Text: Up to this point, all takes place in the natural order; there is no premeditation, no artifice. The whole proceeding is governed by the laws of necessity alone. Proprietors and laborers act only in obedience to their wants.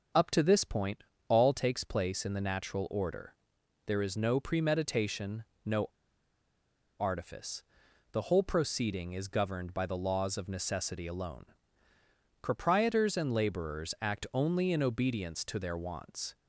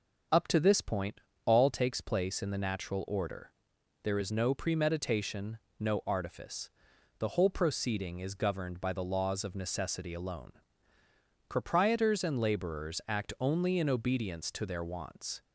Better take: second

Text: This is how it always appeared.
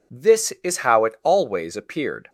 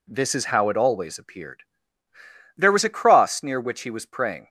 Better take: first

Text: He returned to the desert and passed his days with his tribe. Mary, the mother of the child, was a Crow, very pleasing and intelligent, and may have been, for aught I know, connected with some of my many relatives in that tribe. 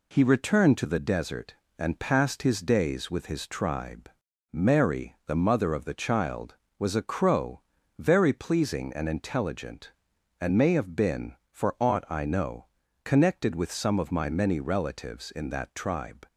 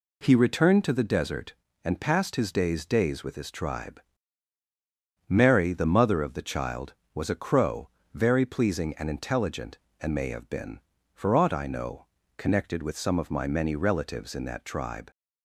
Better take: first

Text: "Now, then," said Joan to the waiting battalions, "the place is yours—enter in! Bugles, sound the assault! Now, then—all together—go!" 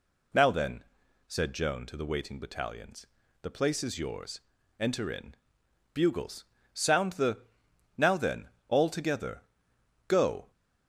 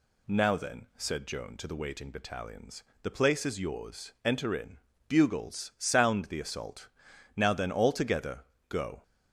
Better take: second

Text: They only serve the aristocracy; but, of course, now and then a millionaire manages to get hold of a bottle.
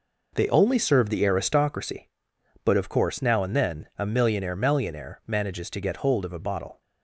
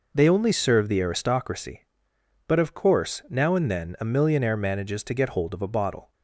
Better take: second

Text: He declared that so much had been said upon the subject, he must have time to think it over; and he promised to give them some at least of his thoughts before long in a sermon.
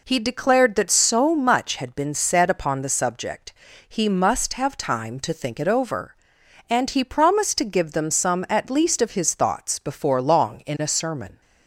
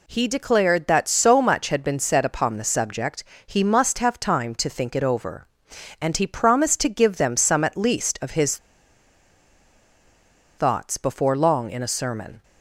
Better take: first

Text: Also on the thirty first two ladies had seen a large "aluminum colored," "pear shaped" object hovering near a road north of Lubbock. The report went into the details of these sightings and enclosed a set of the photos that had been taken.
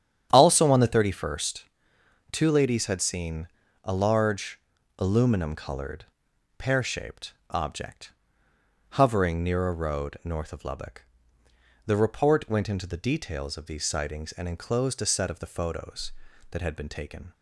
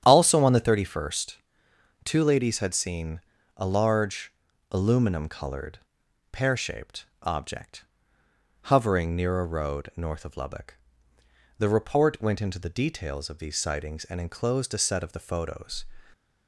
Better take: first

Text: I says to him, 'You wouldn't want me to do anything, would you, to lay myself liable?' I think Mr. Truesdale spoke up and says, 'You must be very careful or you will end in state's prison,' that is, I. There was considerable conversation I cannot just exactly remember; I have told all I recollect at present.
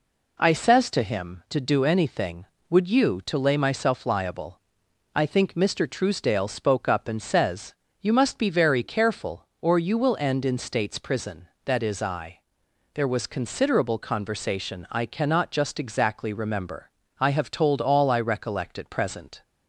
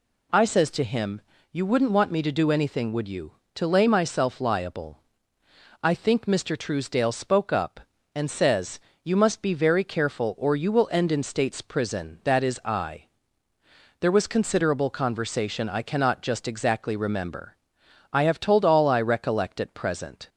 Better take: second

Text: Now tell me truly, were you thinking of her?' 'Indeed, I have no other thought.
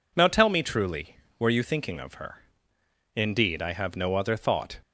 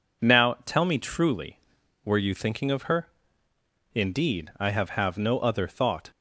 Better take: first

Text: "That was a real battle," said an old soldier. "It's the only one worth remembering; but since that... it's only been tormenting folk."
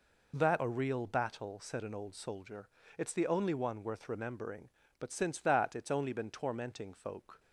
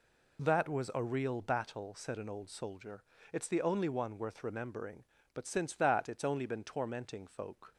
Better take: second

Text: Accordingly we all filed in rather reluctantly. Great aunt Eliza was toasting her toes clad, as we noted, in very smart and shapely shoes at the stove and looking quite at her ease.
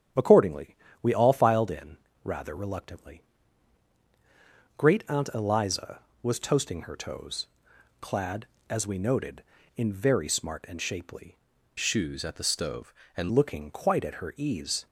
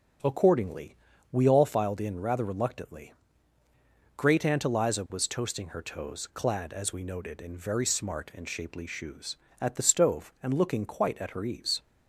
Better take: second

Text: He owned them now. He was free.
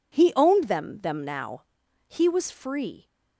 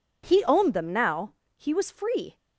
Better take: second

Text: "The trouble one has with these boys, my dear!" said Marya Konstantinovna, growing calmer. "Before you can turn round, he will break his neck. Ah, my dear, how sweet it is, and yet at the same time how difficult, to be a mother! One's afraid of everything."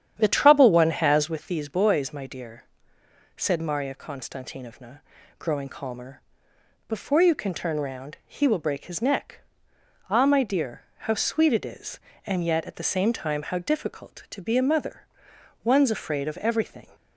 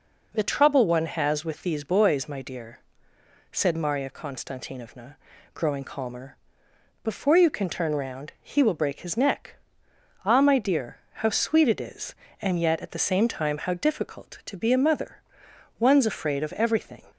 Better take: second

